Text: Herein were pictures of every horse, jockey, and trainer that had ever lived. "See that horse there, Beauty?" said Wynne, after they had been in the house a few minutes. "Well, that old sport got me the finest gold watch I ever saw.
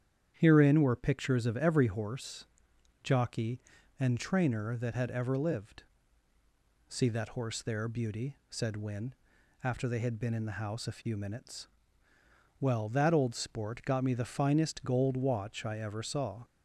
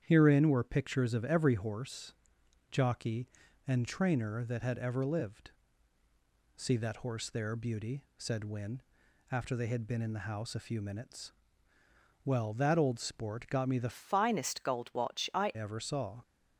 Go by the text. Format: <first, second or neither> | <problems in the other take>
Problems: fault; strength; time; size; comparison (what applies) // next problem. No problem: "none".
first | starts louder than the rest; strong; until 1.0 s; 9 dB; strong in the first // changes voice from "finest" to "I"; from 13.9 to 15.5 s; 1.6 s long